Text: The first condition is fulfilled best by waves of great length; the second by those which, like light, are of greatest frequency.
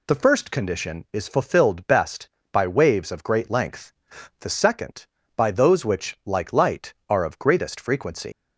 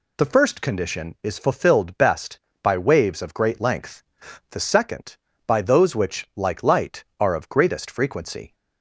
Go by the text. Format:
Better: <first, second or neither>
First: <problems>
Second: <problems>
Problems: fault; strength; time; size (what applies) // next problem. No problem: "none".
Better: second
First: leaves "frequency" unfinished; at 8.3 s; 115 ms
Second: none